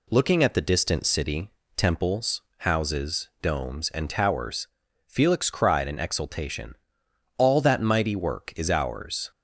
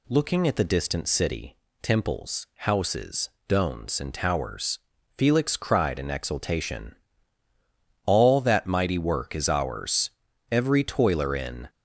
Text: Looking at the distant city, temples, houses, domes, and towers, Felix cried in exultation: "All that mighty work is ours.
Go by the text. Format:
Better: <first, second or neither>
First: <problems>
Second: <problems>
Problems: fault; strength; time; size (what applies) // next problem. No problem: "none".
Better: first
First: none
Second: goes on to say "Every toiler in"; noticeable; from 10.5 s on; 1.1 s long